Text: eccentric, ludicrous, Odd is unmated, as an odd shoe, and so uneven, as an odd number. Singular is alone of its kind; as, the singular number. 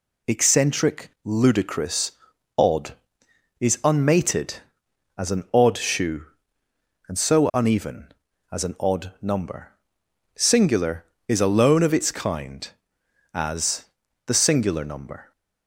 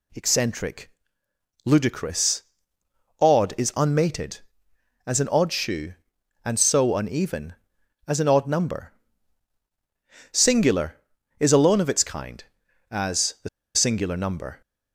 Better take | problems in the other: first | pauses between "the" and "singular"; slight; at 13.4 s; 0.26 s long

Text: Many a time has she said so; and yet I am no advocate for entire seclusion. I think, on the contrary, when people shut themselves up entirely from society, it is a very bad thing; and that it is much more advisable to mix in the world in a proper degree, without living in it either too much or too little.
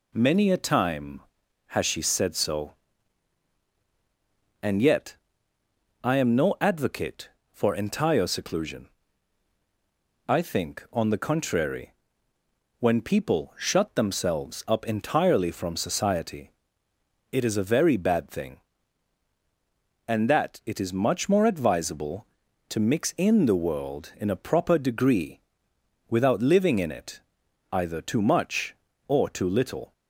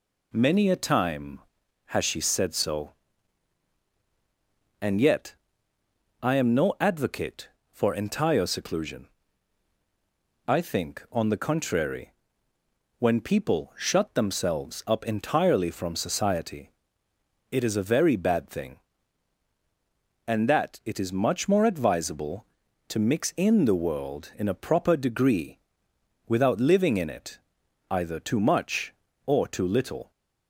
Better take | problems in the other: neither | pauses between "yet" and "I"; noticeable; the same in both // pauses between "it" and "either"; noticeable; the same in both

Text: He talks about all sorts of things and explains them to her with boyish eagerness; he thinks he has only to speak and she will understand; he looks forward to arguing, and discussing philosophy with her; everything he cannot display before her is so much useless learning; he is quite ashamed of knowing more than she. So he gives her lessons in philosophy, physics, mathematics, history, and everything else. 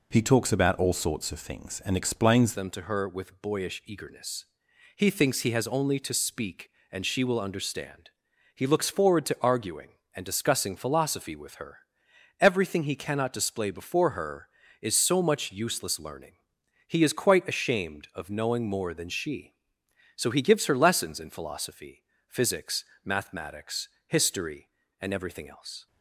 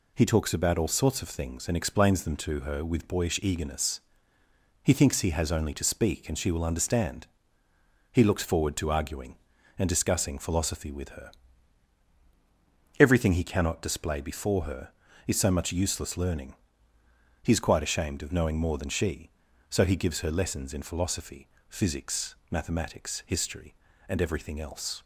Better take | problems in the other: second | changes voice at "them"; from 2.5 s on; 23.3 s long

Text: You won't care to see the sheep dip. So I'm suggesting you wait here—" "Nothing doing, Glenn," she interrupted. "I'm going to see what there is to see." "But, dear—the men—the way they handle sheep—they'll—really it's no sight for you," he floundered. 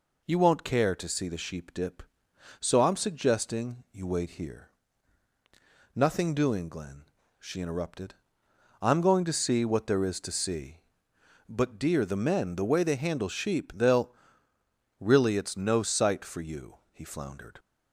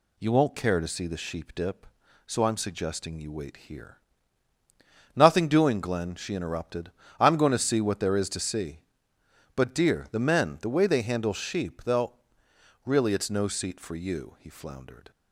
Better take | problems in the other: first | says "seat" for "sight"; at 13.4 s

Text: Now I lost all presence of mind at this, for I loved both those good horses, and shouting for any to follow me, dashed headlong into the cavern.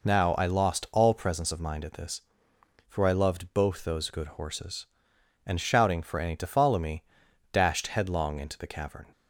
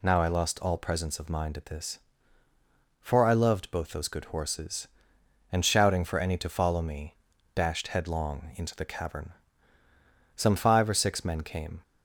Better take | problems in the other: first | goes on to say "Some five or six men came"; from 10.3 s on; 1.4 s long

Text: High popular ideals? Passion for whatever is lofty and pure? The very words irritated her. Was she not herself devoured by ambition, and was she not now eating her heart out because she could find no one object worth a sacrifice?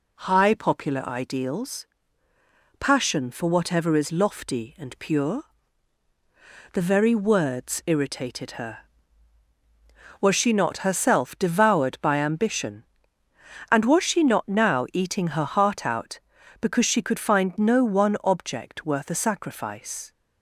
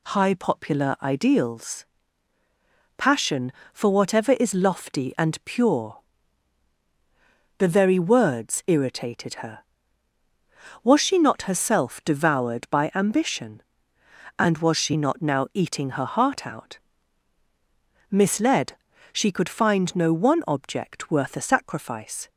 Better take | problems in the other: first | says "misled" for "because"; at 18.1 s

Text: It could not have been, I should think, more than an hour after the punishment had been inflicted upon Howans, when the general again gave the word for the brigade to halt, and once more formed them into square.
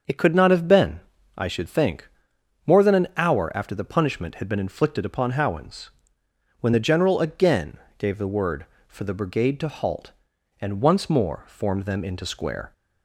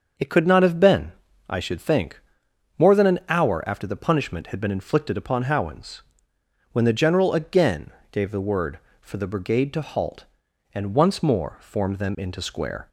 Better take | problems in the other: neither | starts louder than the rest; the same in both // pauses between "again" and "gave"; slight; the same in both

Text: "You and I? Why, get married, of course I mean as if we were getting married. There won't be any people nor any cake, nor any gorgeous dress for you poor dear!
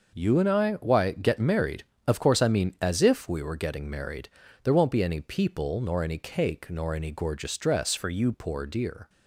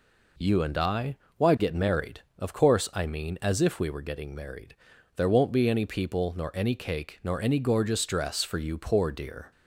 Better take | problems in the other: second | changes voice from "for" to "you"; from 7.9 to 8.3 s; 0.4 s long

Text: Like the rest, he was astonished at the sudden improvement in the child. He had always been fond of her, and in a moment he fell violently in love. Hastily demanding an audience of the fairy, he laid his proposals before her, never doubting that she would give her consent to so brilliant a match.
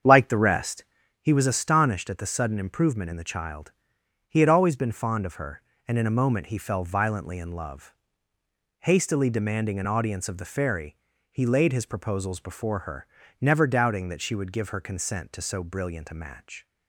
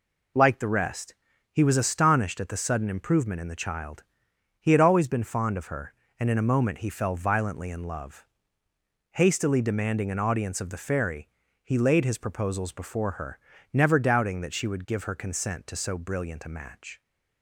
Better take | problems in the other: second | starts louder than the rest; strong; until 1.1 s; 7.5 dB

